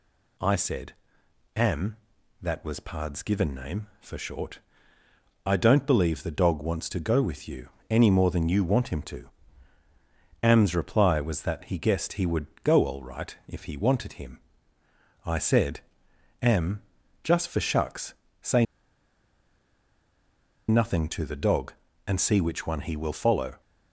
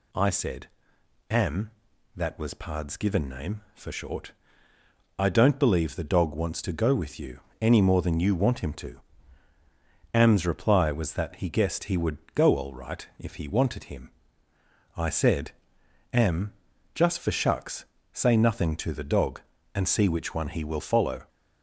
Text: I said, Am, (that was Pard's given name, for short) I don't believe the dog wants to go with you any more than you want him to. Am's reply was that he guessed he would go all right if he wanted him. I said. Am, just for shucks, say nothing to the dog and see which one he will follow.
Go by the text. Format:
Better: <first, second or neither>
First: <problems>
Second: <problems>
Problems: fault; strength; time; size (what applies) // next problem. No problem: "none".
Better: second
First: pauses between "you" and "any"; slight; at 7.6 s; 0.20 s long // pauses between "would" and "go"; slight; at 12.4 s; 0.18 s long // pauses between "say" and "nothing"; strong; at 18.6 s; 2.0 s long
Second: pauses between "you" and "any"; slight; at 7.4 s; 0.20 s long // pauses between "would" and "go"; slight; at 12.1 s; 0.18 s long